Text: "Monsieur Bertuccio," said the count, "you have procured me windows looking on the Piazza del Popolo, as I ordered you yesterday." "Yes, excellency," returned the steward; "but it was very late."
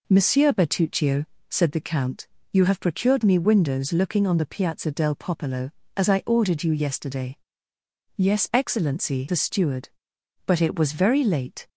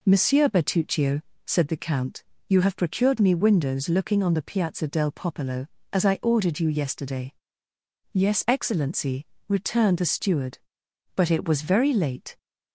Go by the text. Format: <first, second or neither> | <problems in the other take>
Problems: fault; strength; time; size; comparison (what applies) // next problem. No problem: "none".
second | skips "returned"; at 9.2 s